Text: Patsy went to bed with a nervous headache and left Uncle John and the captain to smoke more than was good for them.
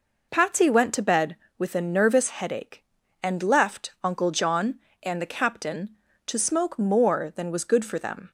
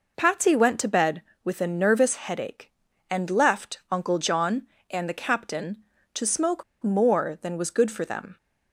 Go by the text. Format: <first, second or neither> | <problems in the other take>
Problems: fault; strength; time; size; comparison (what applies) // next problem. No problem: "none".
first | pauses between "smoke" and "more"; slight; at 6.6 s; 0.19 s long